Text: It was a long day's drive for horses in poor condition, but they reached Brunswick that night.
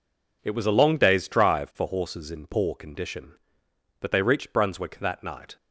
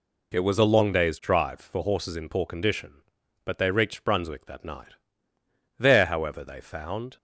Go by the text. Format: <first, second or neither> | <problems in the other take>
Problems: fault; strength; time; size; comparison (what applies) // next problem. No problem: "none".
first | goes on to say "There however they found"; from 5.8 s on; 1.3 s long